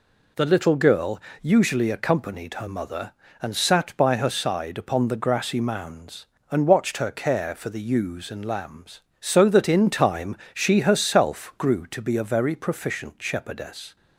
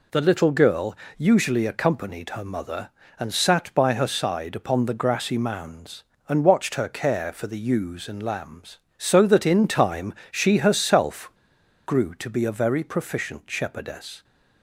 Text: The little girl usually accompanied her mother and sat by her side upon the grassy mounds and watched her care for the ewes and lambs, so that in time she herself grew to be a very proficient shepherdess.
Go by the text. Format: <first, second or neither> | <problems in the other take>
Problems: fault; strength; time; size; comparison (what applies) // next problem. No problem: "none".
first | pauses between "girl" and "usually"; slight; at 0.9 s; 0.22 s long; slight in the first // pauses between "time" and "she"; slight; at 10.1 s; 0.20 s long; slight in the first // pauses between "herself" and "grew"; noticeable; at 11.2 s; 0.56 s long